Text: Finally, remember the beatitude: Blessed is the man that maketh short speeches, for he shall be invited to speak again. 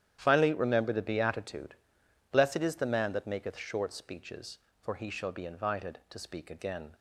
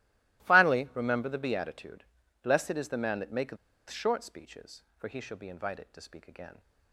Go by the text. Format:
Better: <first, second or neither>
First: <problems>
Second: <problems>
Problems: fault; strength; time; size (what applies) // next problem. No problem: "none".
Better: first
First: starts louder than the rest; strong; until 1.2 s; 10 dB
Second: starts louder than the rest; strong; until 1.4 s; 19 dB // pauses between "maketh" and "short"; slight; at 3.5 s; 0.32 s long